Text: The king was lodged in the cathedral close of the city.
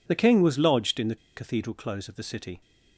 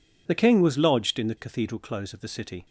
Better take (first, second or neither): second